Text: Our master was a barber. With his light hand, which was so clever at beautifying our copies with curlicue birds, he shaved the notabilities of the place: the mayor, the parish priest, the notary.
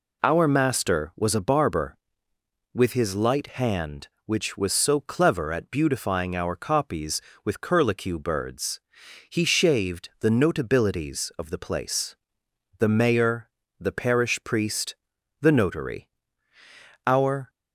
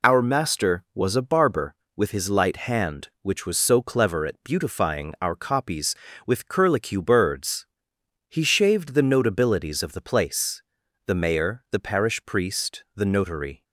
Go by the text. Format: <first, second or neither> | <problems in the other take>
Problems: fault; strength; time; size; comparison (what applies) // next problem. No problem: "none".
second | goes on to say "Our"; slight; from 17.0 s on; 0.44 s long